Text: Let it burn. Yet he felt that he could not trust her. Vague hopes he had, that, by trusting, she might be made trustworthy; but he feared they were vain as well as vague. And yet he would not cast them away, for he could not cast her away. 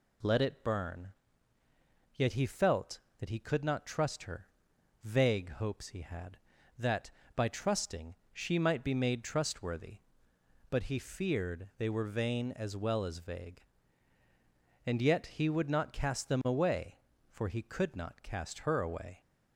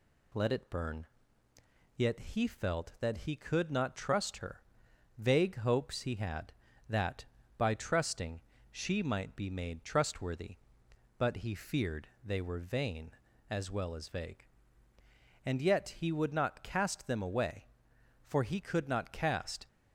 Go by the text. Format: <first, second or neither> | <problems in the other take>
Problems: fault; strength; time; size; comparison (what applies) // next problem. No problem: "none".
first | pauses between "feared" and "they"; slight; at 12.0 s; 0.18 s long // stops before "her away"; at 19.6 s